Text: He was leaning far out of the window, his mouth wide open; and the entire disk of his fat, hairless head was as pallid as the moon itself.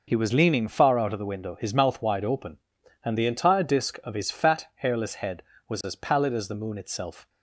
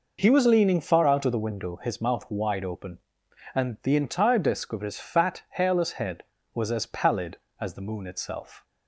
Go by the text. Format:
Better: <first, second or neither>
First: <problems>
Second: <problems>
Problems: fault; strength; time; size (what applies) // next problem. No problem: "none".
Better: neither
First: none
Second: none